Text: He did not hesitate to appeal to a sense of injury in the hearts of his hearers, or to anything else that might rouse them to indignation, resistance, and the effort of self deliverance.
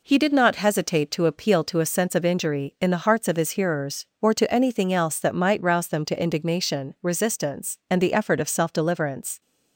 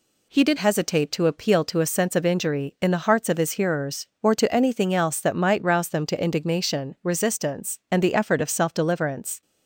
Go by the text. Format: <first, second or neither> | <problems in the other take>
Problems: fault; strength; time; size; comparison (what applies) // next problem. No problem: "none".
first | skips "not"; at 0.5 s